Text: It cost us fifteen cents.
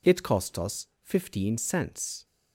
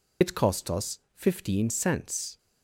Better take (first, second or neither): first